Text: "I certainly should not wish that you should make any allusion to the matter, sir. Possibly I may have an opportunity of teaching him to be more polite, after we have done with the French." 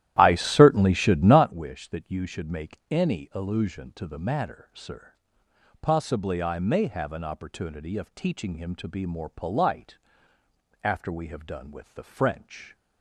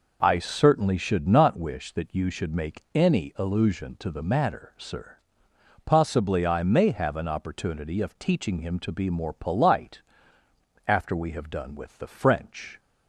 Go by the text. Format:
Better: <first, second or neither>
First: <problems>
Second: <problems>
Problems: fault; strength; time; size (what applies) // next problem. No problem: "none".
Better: second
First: starts louder than the rest; strong; until 1.5 s; 12.5 dB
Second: none